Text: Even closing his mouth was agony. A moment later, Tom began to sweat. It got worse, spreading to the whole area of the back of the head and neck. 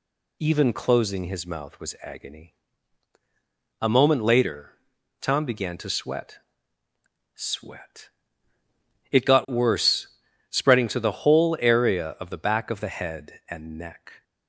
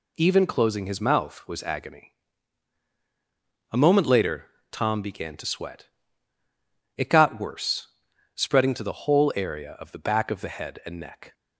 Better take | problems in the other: second | says "sweat" twice; at 7.3 s

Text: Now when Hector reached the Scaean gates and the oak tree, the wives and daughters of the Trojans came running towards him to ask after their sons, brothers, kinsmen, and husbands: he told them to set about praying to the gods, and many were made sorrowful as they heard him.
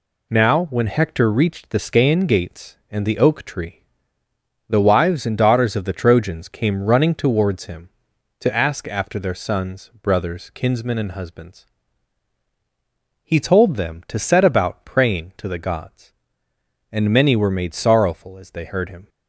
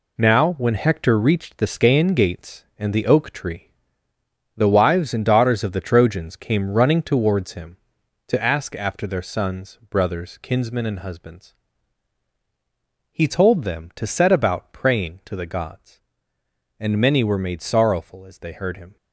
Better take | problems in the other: first | gets quieter; strong; throughout; 8.5 dB

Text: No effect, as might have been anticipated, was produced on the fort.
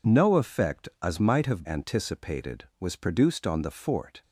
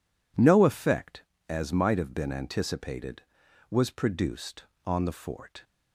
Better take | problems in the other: second | skips "been"; at 1.6 s

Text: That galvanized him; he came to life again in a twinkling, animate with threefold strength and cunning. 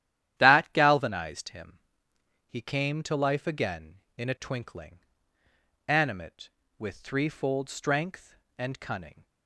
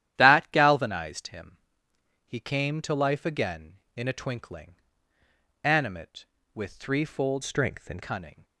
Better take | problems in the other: first | starts louder than the rest; strong; until 1.1 s; 11.5 dB; strong in the first // changes voice from "strength" to "and"; from 7.4 to 8.0 s; 0.6 s long

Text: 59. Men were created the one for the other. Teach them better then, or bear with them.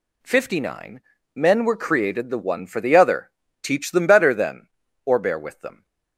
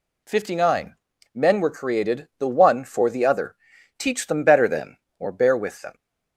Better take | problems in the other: neither | none

